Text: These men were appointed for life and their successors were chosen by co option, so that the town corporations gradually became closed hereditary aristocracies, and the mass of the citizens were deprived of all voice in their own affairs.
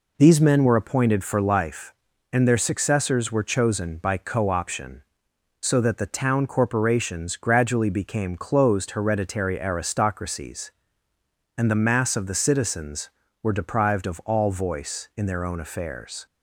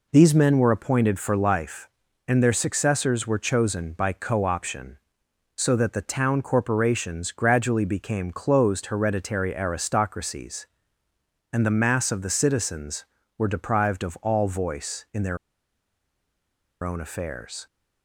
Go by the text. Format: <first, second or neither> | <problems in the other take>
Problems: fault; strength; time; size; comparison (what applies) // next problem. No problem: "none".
first | pauses between "their" and "own"; strong; at 15.3 s; 1.4 s long